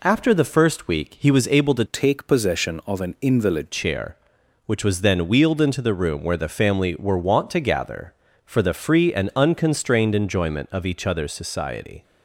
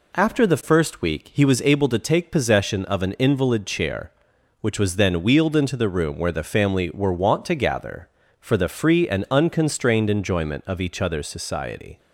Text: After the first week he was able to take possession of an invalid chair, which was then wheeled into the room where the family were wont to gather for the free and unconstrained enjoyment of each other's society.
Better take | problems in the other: second | changes voice from "take" to "invalid"; from 1.8 to 3.7 s; 1.9 s long

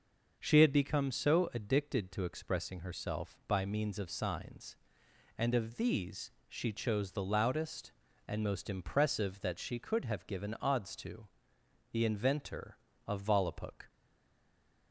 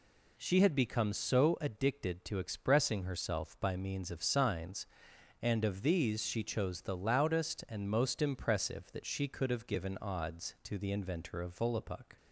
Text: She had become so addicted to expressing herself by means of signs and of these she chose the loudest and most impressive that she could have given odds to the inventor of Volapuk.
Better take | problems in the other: second | starts louder than the rest; until 1.4 s; 6.5 dB // pauses between "these" and "she"; slight; at 6.3 s; 0.18 s long // pauses between "to" and "the"; noticeable; at 11.2 s; 0.66 s long // stays silent after the last word; from 13.8 s on; 1.1 s long

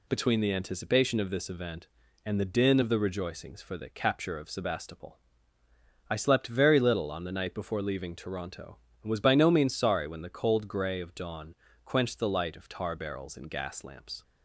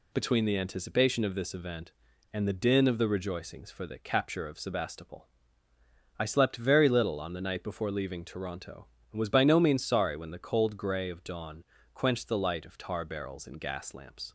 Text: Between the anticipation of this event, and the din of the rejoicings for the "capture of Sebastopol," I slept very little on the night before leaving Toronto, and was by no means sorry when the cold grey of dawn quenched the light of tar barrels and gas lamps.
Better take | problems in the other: neither | pauses between "dawn" and "quenched"; slight; the same in both

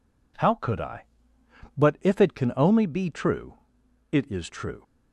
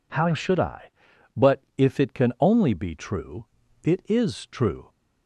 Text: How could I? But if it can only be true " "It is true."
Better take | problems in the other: first | says "should" for "could"; at 0.3 s // pauses between "But" and "if"; slight; at 1.6 s; 0.16 s long

